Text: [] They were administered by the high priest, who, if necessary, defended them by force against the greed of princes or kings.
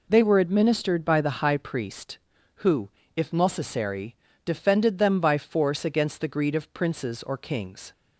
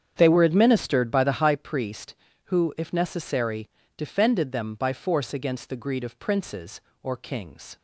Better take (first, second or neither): first